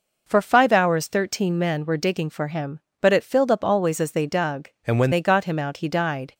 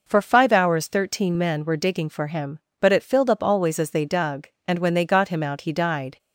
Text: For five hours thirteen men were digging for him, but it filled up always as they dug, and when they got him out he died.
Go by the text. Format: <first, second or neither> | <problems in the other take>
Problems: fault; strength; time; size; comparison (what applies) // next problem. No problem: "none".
second | changes voice from "and" to "when"; from 4.8 to 5.1 s; 0.3 s long